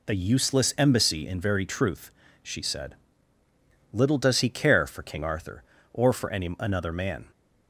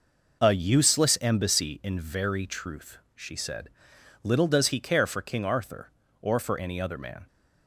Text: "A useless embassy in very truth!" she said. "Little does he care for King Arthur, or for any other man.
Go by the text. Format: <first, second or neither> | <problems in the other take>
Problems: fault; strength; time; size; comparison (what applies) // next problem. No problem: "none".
second | says "another" for "other"; at 6.5 s